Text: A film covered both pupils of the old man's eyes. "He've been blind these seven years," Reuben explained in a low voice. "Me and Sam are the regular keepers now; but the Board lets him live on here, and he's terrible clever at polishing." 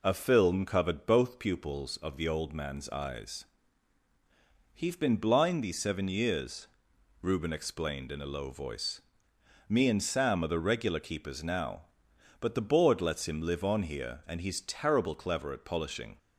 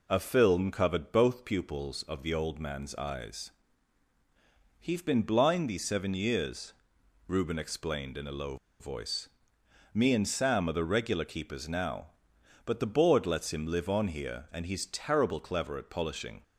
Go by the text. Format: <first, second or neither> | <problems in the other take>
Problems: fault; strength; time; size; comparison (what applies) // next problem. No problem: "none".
first | pauses between "low" and "voice"; slight; at 8.5 s; 0.24 s long